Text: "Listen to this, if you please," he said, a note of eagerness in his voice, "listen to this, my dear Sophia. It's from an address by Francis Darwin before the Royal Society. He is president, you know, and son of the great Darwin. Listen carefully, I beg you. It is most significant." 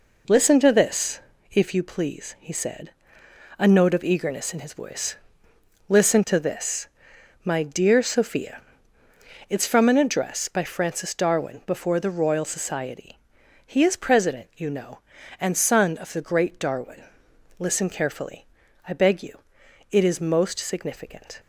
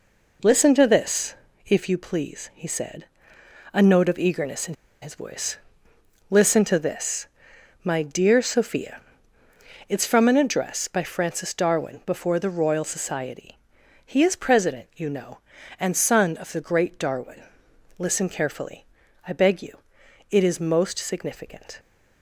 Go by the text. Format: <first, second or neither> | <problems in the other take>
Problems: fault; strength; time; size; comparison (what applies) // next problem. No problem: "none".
first | pauses between "in" and "his"; slight; at 4.7 s; 0.29 s long